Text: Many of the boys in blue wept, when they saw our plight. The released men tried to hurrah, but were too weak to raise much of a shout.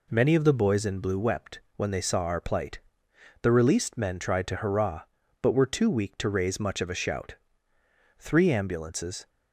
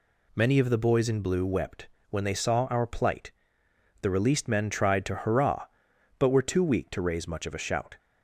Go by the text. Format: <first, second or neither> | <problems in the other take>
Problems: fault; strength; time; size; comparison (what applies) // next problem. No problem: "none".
second | goes on to say "Three ambulances"; noticeable; from 8.1 s on; 1.1 s long